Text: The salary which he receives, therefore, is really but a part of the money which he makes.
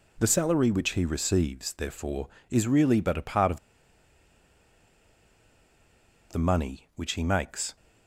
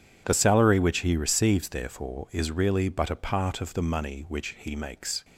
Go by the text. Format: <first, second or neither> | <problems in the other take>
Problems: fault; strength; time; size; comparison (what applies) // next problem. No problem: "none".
second | pauses between "of" and "the"; strong; at 3.5 s; 2.7 s long